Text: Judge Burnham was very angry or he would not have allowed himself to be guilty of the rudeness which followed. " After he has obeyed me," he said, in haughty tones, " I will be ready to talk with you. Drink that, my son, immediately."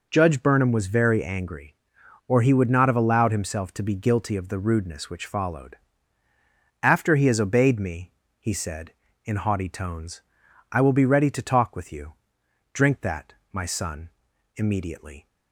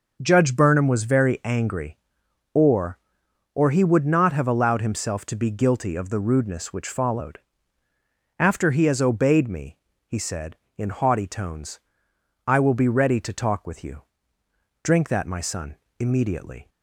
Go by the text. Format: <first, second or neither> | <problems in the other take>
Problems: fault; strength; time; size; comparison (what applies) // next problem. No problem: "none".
first | starts louder than the rest; noticeable; until 1.2 s; 6 dB // says "or" twice; at 3.5 s